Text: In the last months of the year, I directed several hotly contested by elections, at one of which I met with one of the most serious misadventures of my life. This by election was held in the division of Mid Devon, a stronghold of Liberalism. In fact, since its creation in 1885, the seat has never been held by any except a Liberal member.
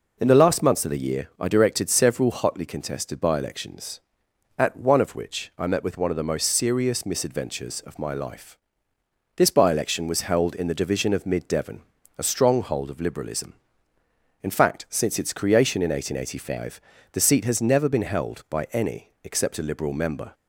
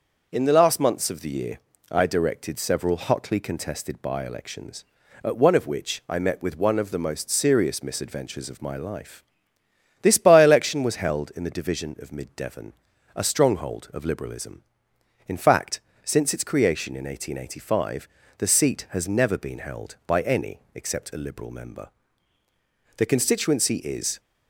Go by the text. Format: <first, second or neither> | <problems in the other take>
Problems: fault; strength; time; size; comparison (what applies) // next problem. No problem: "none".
first | starts louder than the rest; until 1.3 s; 6 dB // goes on to say "The constituency is"; noticeable; from 22.9 s on; 1.2 s long